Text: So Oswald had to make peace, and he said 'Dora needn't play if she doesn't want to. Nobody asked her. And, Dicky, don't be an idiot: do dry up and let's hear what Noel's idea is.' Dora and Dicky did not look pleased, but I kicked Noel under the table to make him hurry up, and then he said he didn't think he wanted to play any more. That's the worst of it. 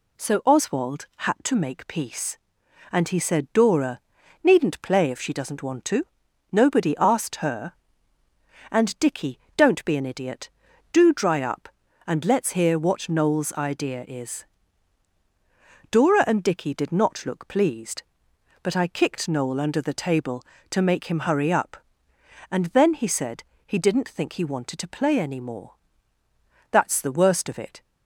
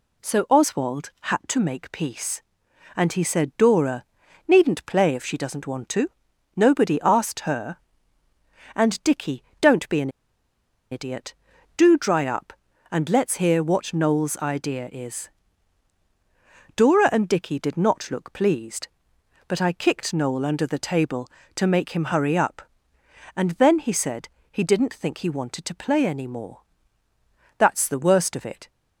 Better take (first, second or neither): first